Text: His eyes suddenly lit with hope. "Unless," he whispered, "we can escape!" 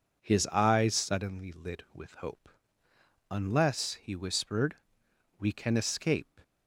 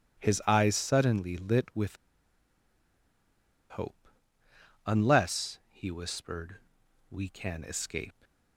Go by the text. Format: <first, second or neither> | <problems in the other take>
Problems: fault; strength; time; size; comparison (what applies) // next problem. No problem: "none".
first | pauses between "with" and "hope"; strong; at 1.9 s; 1.7 s long